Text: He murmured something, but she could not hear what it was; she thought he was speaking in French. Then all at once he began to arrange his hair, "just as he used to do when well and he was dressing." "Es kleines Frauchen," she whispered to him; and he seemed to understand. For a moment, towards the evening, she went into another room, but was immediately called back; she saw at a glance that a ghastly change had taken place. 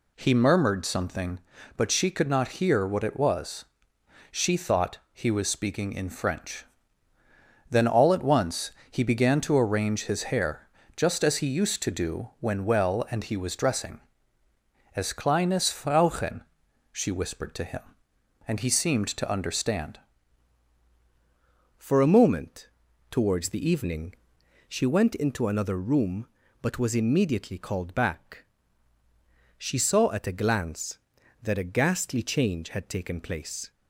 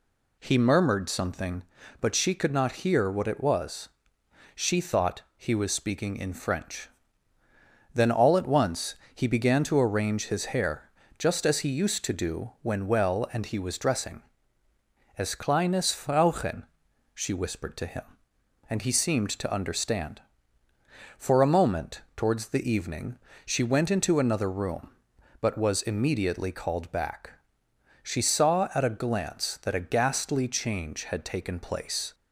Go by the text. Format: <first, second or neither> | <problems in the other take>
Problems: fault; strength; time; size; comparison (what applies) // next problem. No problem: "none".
second | pauses between "once" and "he"; slight; at 8.7 s; 0.18 s long; slight in the second // changes voice at "For"; from 21.7 s on; 12.0 s long